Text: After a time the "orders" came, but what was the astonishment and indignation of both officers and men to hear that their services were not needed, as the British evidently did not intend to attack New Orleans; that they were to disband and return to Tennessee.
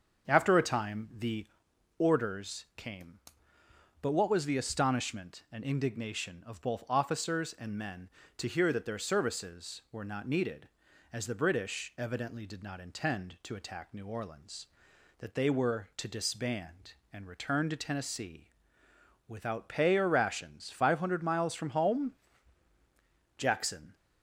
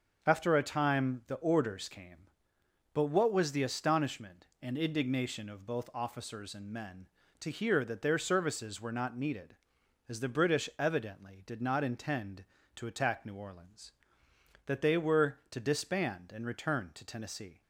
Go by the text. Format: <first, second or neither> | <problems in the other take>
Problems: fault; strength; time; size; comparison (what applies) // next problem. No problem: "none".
second | starts louder than the rest; until 1.3 s; 6.5 dB; also in the second // pauses between "the" and "orders"; noticeable; at 1.4 s; 0.52 s long // goes on to say "Without pay or rations five hundred miles from home Jackson"; strong; from 19.2 s on; 4.6 s long